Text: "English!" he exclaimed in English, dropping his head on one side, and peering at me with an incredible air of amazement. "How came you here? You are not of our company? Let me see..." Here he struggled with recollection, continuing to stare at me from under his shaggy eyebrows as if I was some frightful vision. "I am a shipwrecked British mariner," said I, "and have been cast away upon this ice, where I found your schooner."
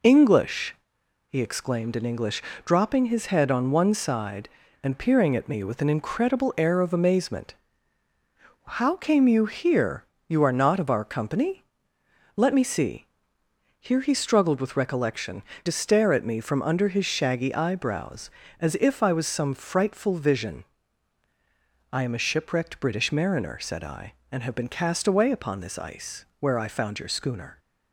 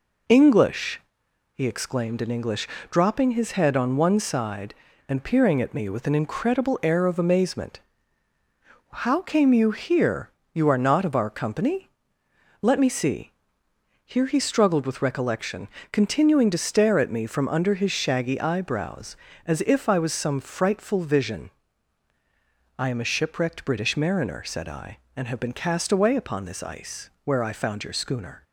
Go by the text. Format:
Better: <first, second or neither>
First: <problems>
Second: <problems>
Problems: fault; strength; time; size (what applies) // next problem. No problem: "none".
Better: second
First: skips "continuing"; at 15.5 s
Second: none